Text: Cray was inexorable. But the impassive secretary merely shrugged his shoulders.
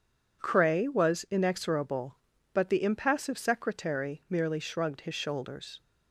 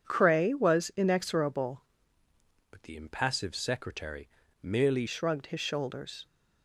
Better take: first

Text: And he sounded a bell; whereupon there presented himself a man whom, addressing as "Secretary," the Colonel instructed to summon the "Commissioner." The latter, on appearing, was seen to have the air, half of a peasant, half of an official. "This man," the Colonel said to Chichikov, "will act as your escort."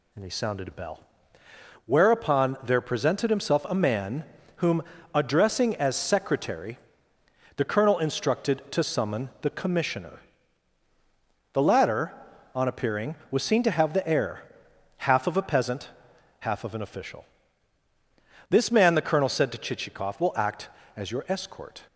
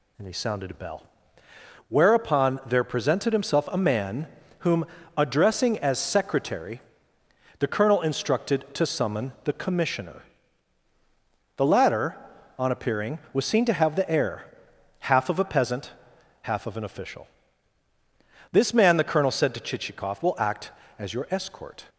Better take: neither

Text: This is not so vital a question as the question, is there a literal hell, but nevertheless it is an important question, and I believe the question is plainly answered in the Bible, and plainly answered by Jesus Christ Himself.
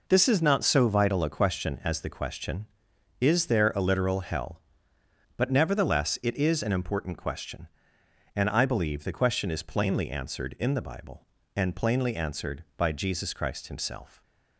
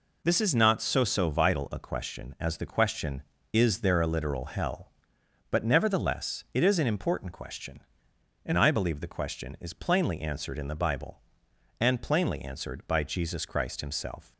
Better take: first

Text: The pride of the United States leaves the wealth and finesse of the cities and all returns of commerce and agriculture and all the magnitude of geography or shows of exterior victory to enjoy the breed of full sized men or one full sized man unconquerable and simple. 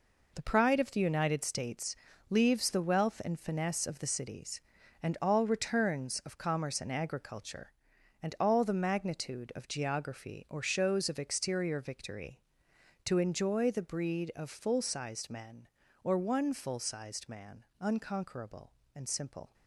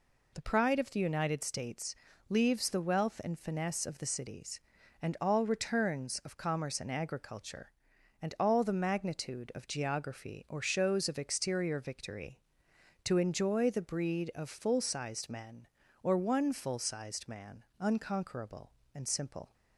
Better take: second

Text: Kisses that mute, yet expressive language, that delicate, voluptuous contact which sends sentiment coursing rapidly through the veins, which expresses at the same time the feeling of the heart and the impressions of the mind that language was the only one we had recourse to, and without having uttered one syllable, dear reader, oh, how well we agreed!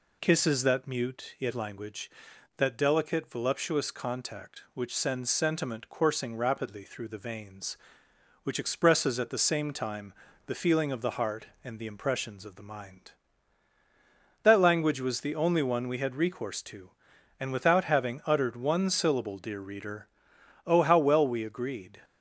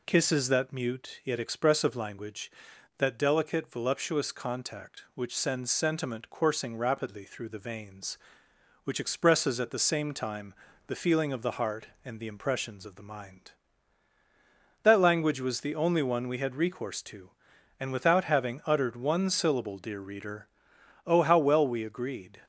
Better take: second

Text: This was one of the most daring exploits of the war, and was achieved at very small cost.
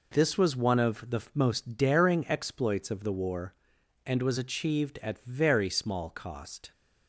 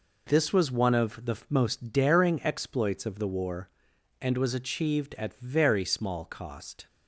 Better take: neither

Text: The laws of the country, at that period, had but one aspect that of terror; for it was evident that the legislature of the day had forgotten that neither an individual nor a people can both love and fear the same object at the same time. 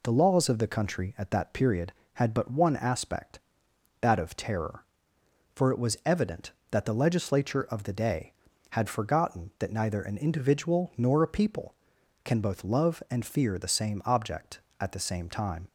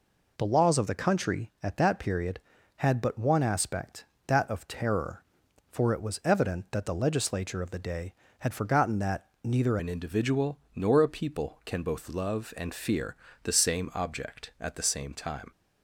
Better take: first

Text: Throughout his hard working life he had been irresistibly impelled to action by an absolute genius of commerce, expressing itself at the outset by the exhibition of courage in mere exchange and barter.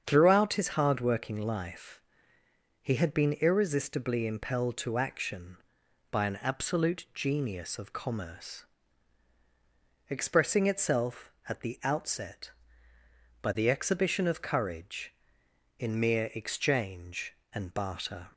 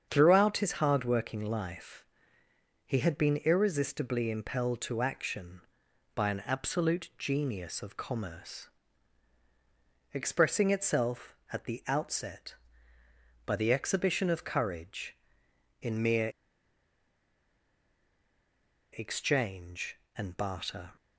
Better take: first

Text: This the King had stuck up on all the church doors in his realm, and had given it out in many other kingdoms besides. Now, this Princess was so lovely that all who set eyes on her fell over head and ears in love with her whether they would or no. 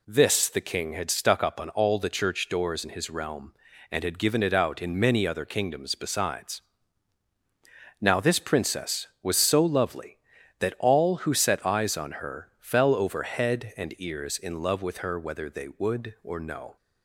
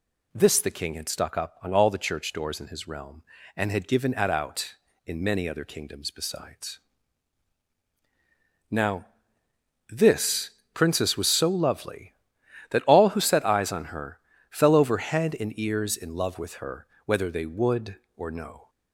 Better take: first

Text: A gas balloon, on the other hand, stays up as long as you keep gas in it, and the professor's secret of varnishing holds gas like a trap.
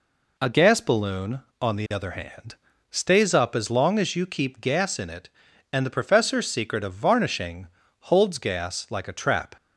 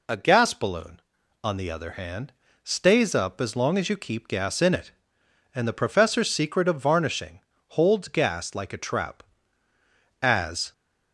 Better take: first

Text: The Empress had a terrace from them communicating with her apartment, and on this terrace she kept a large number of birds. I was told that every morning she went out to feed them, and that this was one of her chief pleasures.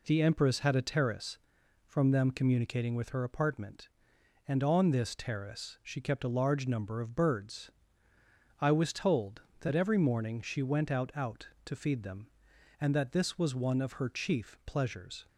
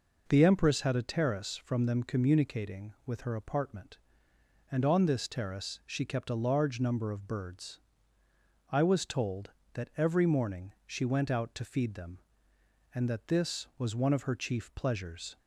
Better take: second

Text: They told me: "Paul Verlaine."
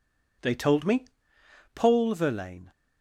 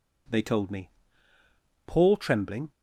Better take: first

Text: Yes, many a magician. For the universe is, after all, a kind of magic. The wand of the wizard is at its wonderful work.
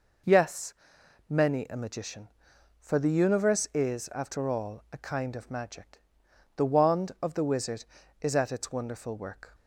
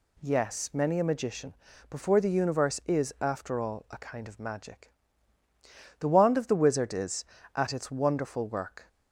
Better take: first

